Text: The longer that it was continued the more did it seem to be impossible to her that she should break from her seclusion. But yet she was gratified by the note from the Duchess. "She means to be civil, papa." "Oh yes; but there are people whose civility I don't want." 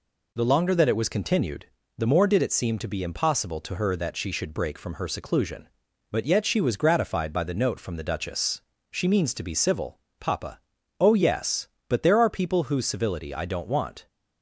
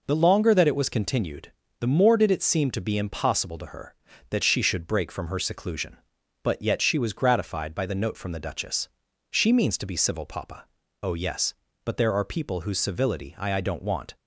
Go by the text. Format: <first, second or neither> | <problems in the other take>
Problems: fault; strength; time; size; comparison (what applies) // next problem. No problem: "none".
first | pauses between "continued" and "the"; slight; at 1.5 s; 0.26 s long; slight in the first // says "I" twice; at 13.5 s